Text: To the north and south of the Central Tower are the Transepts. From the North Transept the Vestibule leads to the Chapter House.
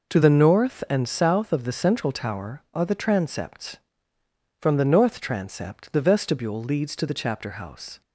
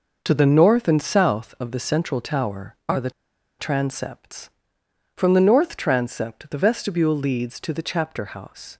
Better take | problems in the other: first | pauses between "the" and "Transepts"; noticeable; at 3.0 s; 0.49 s long

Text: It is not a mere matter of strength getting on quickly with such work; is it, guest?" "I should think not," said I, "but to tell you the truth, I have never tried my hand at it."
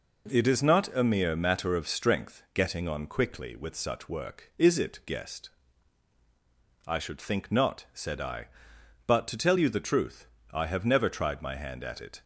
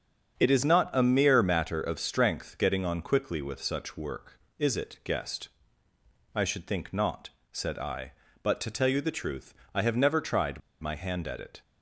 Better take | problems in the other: first | starts louder than the rest; strong; until 1.4 s; 7 dB // pauses between "tried" and "my"; slight; at 10.6 s; 0.20 s long

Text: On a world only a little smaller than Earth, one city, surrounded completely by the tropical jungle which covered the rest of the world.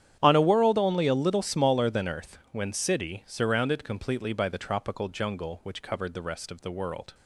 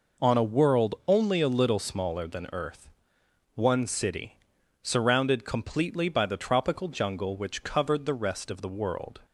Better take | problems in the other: second | starts louder than the rest; strong; until 1.2 s; 10 dB // says "when" for "one"; at 2.5 s

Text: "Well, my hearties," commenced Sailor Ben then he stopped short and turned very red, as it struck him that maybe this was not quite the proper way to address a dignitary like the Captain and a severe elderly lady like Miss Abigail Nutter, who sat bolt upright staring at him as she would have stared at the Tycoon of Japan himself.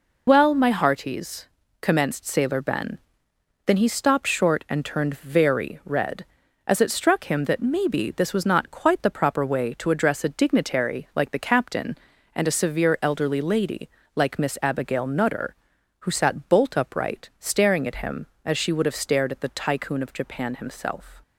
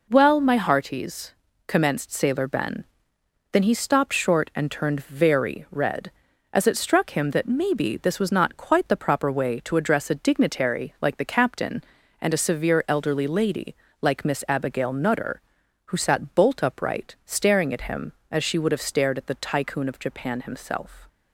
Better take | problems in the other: second | loses the start of "Well"; at 0.2 s; 35 ms // pauses between "Ben" and "then"; noticeable; at 2.9 s; 0.66 s long; noticeable in the second // pauses between "lady" and "like"; slight; at 13.8 s; 0.26 s long; slight in the second

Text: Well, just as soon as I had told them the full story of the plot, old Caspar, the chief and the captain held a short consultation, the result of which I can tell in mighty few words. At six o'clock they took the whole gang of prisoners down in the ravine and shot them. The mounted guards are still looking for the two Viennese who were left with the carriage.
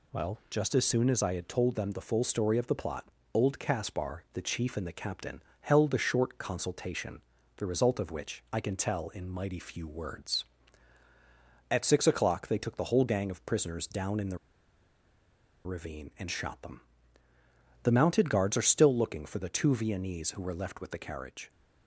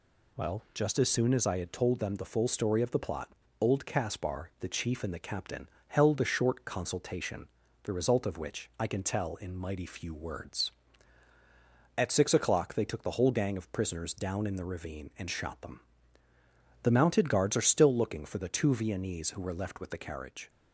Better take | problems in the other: second | pauses between "captain" and "held"; slight; at 5.4 s; 0.18 s long; slight in the second // pauses between "the" and "ravine"; strong; at 14.3 s; 1.2 s long

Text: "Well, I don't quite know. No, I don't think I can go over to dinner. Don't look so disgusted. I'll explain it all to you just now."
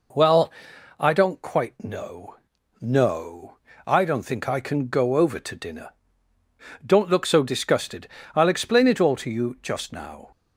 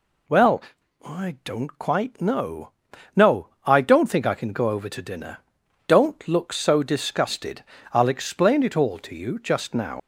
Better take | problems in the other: first | leaves "now" unfinished; at 9.9 s; 115 ms

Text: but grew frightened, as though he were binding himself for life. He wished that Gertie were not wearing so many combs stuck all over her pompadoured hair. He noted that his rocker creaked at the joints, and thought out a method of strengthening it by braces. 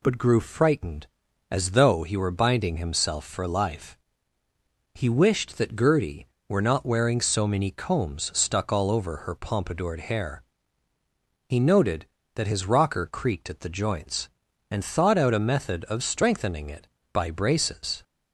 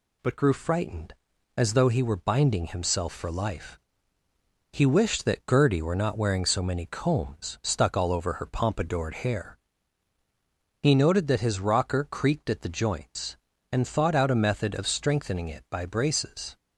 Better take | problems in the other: neither | none

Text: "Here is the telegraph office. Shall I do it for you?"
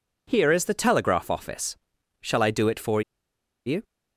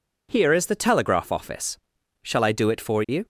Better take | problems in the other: second | pauses between "for" and "you"; noticeable; at 3.0 s; 0.65 s long

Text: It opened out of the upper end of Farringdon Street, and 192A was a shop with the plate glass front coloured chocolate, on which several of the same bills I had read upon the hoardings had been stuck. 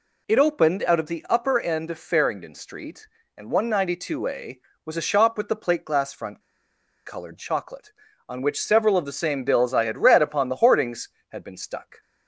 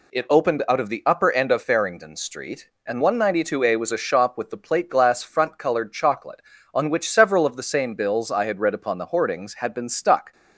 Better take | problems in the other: second | pauses between "front" and "coloured"; noticeable; at 6.4 s; 0.65 s long

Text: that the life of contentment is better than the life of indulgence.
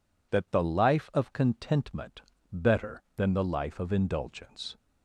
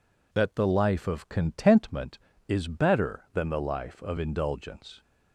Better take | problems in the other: second | skips "is"; at 2.3 s

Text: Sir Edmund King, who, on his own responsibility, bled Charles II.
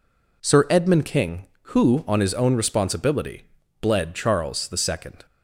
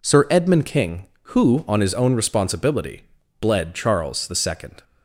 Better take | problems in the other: neither | none

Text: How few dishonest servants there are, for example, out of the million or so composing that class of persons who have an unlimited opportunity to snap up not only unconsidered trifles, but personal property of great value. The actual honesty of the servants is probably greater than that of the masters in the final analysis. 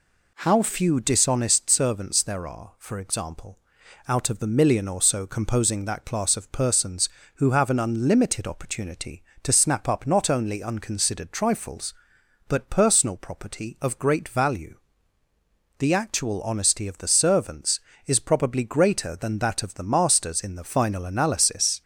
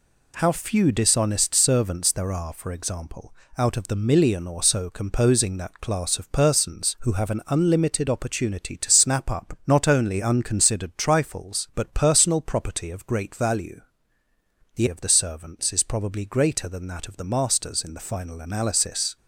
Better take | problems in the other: first | skips "actual honesty"; at 14.8 s

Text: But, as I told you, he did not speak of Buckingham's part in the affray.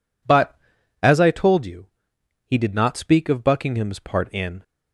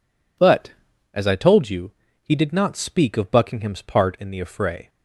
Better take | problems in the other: second | stops before "the affray"; at 4.6 s

